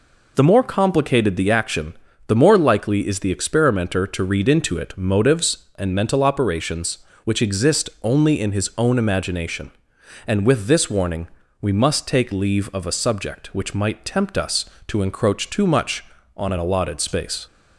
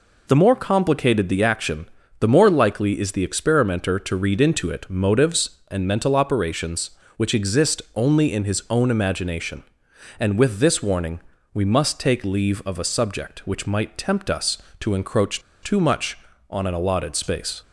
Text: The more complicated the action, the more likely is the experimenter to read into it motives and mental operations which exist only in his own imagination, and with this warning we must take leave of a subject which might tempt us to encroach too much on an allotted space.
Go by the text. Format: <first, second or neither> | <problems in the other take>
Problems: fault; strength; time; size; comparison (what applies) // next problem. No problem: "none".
first | pauses between "exist" and "only"; slight; at 7.8 s; 0.16 s long; slight in the first // pauses between "warning" and "we"; slight; at 11.2 s; 0.34 s long; slight in the first // pauses between "encroach" and "too"; slight; at 15.4 s; 0.22 s long